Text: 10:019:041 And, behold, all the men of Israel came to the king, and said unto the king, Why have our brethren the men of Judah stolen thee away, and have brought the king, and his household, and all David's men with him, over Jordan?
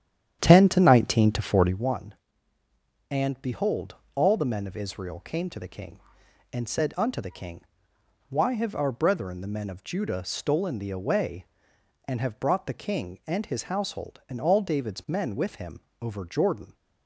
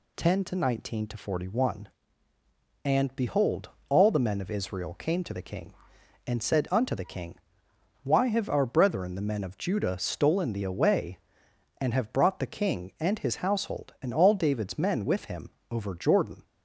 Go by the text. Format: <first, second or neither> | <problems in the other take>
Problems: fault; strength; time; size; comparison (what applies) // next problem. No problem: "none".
second | starts louder than the rest; strong; until 1.9 s; 10 dB